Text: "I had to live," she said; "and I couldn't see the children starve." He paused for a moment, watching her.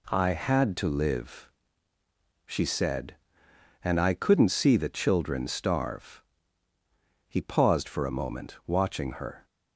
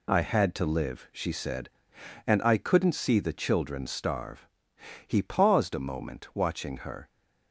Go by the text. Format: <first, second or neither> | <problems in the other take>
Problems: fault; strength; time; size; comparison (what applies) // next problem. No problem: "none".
first | skips "for"; at 5.7 s